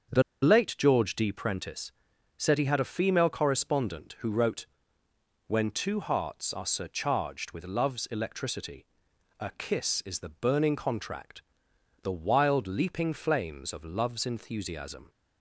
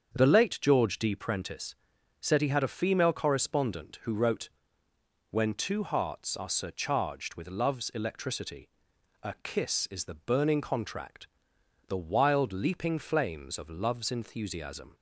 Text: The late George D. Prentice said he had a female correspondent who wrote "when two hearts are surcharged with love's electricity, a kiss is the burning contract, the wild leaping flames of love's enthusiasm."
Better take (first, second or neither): second